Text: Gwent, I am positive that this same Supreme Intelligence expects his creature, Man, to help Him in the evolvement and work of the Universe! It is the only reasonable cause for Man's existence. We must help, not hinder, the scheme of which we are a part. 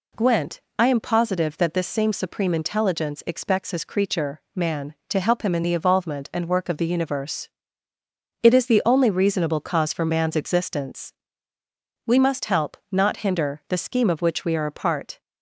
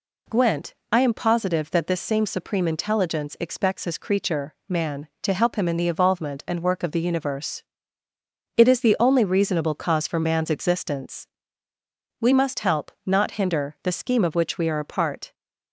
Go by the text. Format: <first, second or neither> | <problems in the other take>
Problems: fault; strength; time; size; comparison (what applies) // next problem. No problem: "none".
neither | none